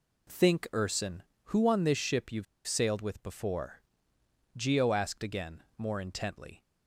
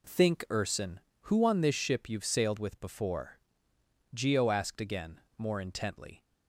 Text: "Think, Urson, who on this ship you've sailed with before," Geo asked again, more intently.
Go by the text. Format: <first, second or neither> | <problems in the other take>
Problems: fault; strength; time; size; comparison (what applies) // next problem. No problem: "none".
second | pauses between "you've" and "sailed"; slight; at 2.4 s; 0.22 s long